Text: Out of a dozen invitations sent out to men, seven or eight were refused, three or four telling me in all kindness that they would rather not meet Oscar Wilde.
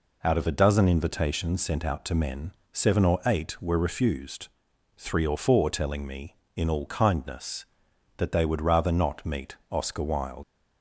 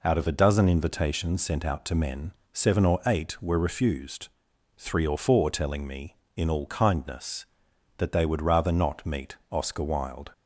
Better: second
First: pauses between "meet" and "Oscar"; slight; at 9.5 s; 0.16 s long // leaves "Wilde" unfinished; at 10.4 s; 85 ms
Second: pauses between "meet" and "Oscar"; slight; at 9.3 s; 0.16 s long

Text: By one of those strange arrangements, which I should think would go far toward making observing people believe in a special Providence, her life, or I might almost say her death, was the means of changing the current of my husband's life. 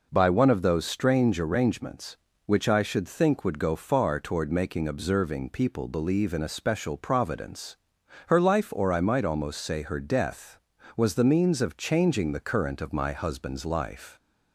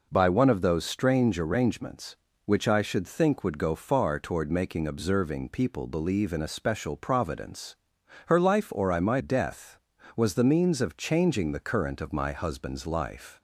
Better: first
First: none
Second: skips "almost say her"; at 9.2 s

